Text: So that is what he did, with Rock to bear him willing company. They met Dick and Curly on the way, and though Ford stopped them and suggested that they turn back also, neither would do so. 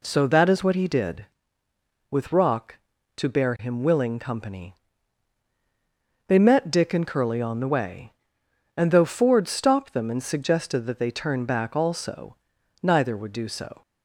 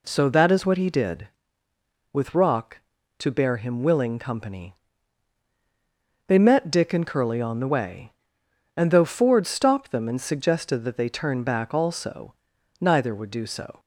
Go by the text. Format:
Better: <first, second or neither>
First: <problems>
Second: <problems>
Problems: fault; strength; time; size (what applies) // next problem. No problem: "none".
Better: neither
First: none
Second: none